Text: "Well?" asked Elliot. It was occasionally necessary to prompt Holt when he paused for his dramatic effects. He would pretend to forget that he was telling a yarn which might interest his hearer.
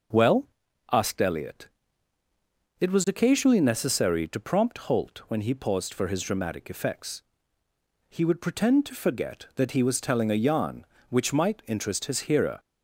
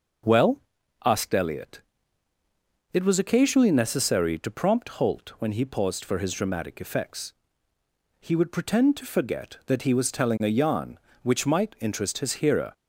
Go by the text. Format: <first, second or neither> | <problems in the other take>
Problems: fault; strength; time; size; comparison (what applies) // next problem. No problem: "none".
neither | starts louder than the rest; noticeable; the same in both